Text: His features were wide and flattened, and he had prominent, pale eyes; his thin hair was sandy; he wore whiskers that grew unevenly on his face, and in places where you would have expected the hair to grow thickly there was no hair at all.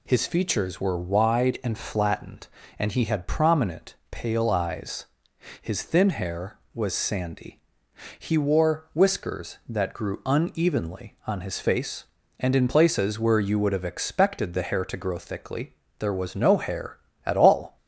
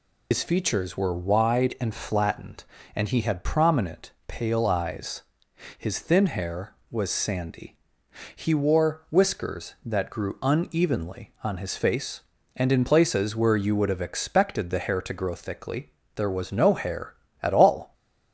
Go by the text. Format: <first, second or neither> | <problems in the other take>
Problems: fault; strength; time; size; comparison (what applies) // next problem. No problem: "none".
first | loses the start of "His"; at 0.3 s; 75 ms // pauses between "thickly" and "there"; slight; at 15.8 s; 0.26 s long; slight in the first